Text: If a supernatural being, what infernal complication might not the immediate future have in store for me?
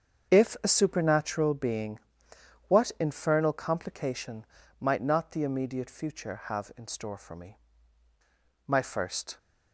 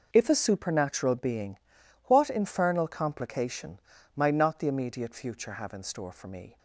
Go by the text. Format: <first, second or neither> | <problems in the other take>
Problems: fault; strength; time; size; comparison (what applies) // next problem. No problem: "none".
second | starts louder than the rest; strong; until 1.3 s; 7 dB // pauses between "complication" and "might"; slight; at 4.4 s; 0.36 s long; slight in the second // goes on to say "My first"; noticeable; from 8.6 s on; 0.72 s long